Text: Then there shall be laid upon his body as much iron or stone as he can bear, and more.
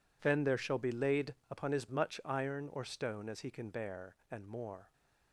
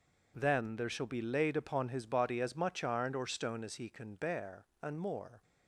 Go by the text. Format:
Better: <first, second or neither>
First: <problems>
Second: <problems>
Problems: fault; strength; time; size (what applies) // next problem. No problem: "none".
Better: second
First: skips "body as"; at 1.8 s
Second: none